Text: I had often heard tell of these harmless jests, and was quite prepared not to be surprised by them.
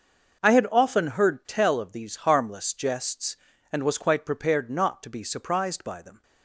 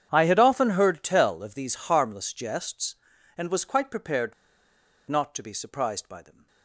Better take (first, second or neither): first